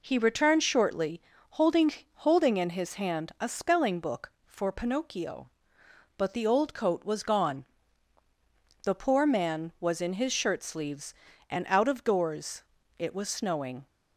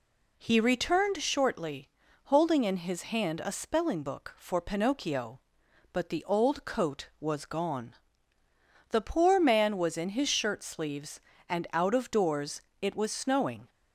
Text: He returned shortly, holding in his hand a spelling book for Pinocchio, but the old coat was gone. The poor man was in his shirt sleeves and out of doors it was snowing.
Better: second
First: says "holding" twice; at 2.1 s // pauses between "doors" and "it"; slight; at 12.6 s; 0.34 s long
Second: pauses between "doors" and "it"; slight; at 12.6 s; 0.20 s long

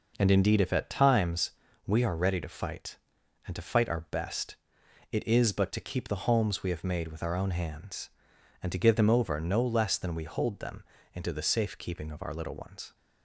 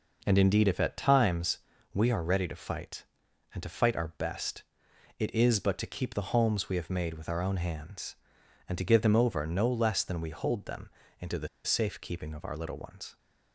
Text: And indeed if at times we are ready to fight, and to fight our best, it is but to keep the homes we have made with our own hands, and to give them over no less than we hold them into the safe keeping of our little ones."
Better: first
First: pauses between "times" and "we"; slight; at 1.5 s; 0.34 s long // pauses between "them" and "into"; slight; at 10.8 s; 0.30 s long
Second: pauses between "times" and "we"; slight; at 1.5 s; 0.34 s long // pauses between "them" and "into"; slight; at 10.8 s; 0.30 s long // pauses between "the" and "safe"; slight; at 11.4 s; 0.17 s long

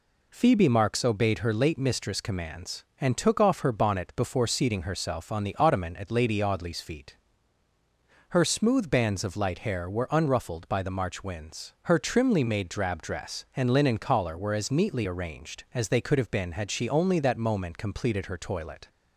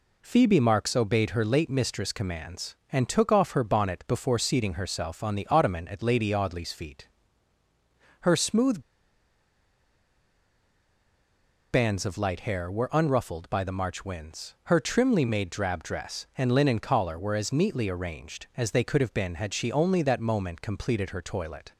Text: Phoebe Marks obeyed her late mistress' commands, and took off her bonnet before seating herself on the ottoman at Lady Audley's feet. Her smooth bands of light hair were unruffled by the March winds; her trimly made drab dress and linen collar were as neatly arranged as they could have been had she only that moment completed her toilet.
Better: first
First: none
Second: pauses between "smooth" and "bands"; strong; at 8.8 s; 2.9 s long

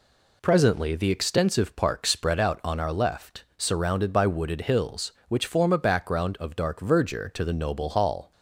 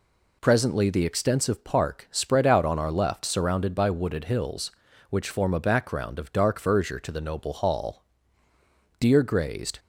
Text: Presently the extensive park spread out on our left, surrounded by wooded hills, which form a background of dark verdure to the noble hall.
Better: first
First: none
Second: goes on to say "Deer grazed"; noticeable; from 8.9 s on; 0.80 s long

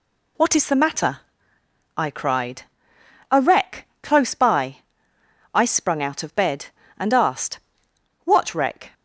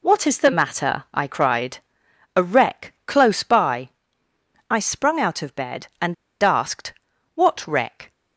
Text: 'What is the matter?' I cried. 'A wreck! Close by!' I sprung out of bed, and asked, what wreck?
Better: first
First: none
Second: pauses between "and" and "asked"; slight; at 6.1 s; 0.28 s long

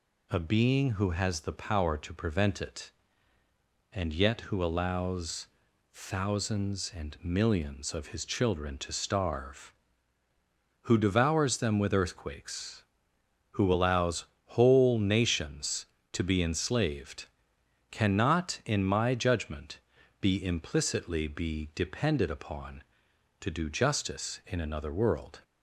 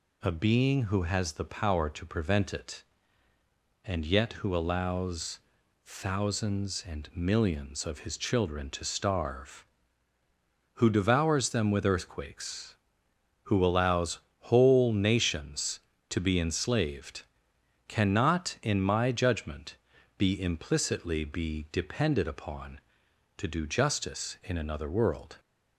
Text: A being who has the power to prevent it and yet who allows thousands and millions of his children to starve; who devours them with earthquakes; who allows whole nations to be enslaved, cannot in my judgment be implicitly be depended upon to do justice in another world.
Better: neither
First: pauses between "allows" and "thousands"; noticeable; at 5.4 s; 0.46 s long // pauses between "allows" and "whole"; slight; at 14.2 s; 0.20 s long // pauses between "judgment" and "be"; at 19.7 s; 0.42 s long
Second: pauses between "allows" and "thousands"; noticeable; at 5.3 s; 0.46 s long // pauses between "allows" and "whole"; slight; at 14.1 s; 0.20 s long // pauses between "judgment" and "be"; at 19.7 s; 0.42 s long

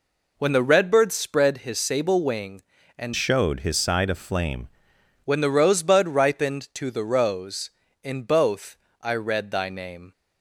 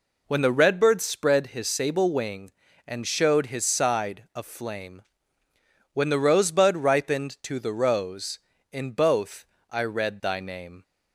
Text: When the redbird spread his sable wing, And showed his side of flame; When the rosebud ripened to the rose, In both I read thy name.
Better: second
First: changes voice from "showed" to "flame"; from 3.1 to 4.6 s; 1.5 s long // pauses between "both" and "I"; slight; at 8.7 s; 0.26 s long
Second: pauses between "both" and "I"; slight; at 9.4 s; 0.26 s long

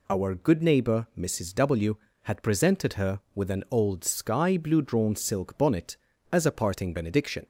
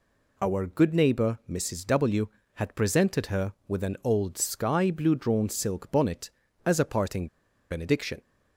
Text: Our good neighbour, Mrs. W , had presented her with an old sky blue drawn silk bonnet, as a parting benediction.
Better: first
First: none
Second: pauses between "parting" and "benediction"; at 7.2 s; 0.43 s long

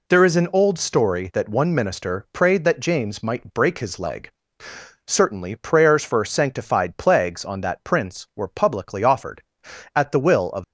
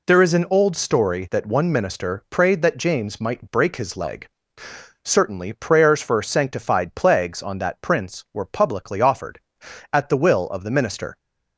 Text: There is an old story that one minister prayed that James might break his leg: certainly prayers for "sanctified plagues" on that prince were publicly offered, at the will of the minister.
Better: second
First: stops before "the minister"; at 10.6 s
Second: none

